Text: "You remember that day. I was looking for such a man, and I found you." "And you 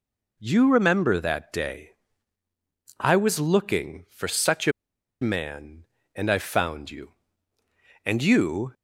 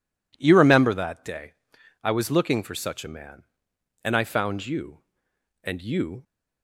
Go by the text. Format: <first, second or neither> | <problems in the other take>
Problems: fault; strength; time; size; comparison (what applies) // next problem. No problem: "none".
second | pauses between "a" and "man"; noticeable; at 4.7 s; 0.49 s long